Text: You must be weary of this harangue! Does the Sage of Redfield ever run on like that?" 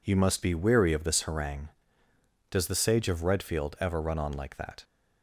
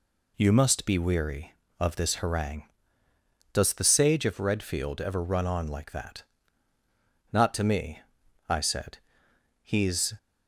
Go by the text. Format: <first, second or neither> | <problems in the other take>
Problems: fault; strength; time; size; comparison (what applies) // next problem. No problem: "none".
first | goes on to say "Not to me I said He's"; strong; from 7.3 s on; 2.8 s long